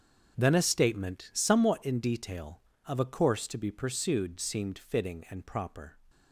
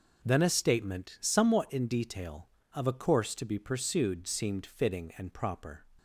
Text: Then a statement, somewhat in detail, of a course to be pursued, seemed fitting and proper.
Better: second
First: gets quieter; strong; throughout; 14 dB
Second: none

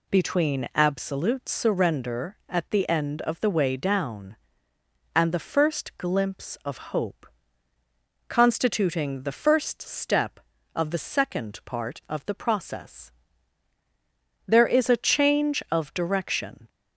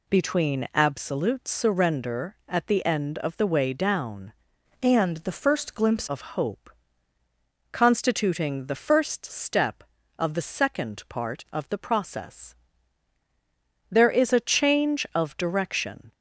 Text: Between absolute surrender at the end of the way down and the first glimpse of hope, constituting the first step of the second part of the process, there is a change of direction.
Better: first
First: none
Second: changes voice from "and" to "glimpse"; from 4.8 to 6.0 s; 1.2 s long

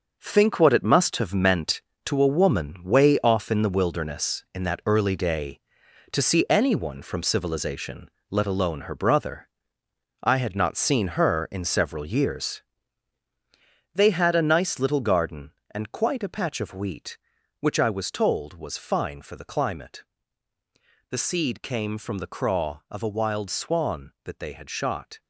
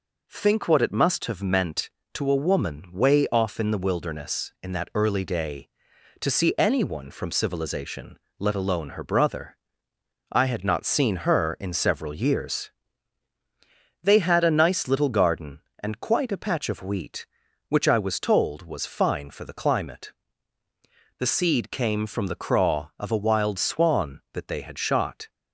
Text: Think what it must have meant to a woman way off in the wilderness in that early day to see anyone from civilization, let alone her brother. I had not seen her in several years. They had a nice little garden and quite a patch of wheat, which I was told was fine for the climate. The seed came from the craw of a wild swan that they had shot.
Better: second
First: gets quieter; strong; throughout; 9 dB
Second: none

